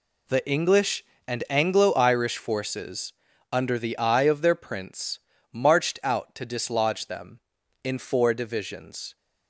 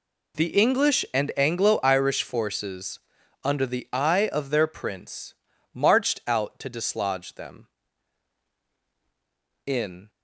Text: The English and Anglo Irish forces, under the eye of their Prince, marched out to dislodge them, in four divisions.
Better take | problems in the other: first | stops before "four divisions"; at 10.0 s

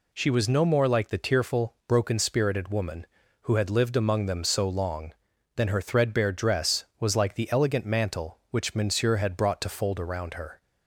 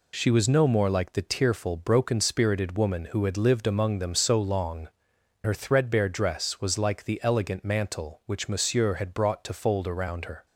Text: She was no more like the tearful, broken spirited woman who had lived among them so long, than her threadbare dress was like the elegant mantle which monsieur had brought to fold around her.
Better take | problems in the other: first | skips "than"; at 5.1 s

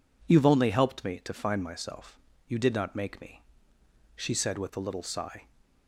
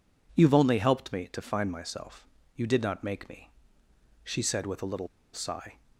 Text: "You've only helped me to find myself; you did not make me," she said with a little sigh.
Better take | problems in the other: first | pauses between "little" and "sigh"; slight; at 5.0 s; 0.26 s long

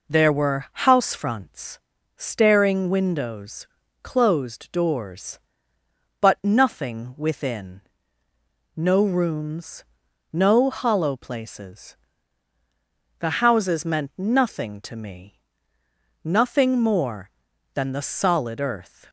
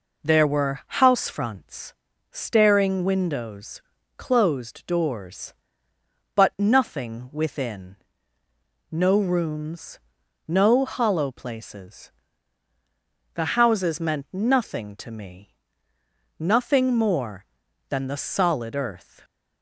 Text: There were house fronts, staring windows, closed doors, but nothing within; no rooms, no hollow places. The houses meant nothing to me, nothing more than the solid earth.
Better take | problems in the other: neither | pauses between "were" and "house"; slight; the same in both

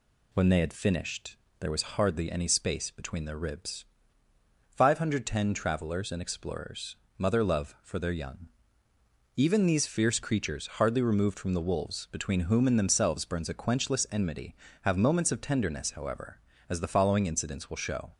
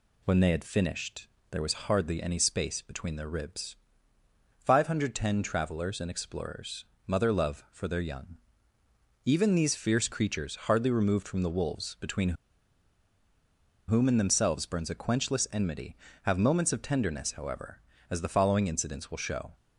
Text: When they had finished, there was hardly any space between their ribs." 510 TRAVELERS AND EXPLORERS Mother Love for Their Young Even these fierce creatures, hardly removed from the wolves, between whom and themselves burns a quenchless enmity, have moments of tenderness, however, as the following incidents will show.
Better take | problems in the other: first | pauses between "EXPLORERS" and "Mother"; slight; at 6.8 s; 0.22 s long; slight in the first // pauses between "Young" and "Even"; noticeable; at 8.3 s; 0.88 s long; noticeable in the first // pauses between "between" and "whom"; strong; at 12.3 s; 1.5 s long

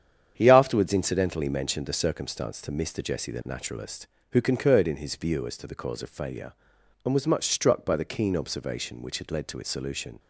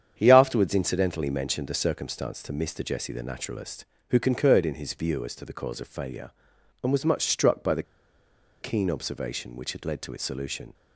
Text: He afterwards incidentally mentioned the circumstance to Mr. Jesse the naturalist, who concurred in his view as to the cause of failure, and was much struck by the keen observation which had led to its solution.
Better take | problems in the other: first | starts louder than the rest; strong; until 1.1 s; 8.5 dB; strong in the first // pauses between "the" and "keen"; noticeable; at 7.8 s; 0.77 s long

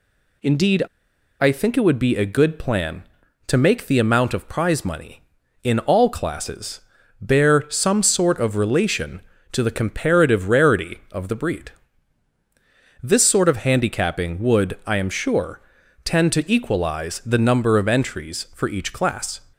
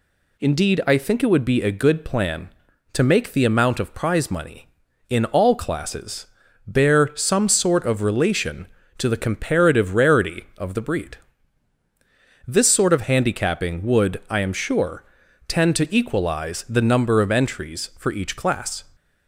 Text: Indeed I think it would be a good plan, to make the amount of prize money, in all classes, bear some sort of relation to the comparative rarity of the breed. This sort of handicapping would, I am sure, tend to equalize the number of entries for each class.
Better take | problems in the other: second | pauses between "Indeed" and "I"; noticeable; at 0.8 s; 0.56 s long

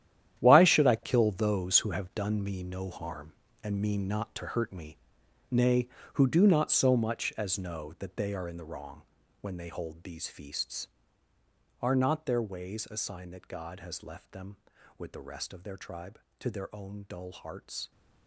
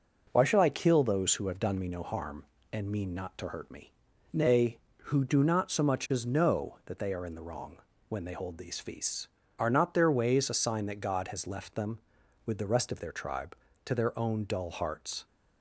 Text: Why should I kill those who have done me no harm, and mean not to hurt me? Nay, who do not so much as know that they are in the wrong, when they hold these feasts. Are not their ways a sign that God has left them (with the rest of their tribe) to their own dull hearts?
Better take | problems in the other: second | gets quieter; strong; throughout; 12.5 dB

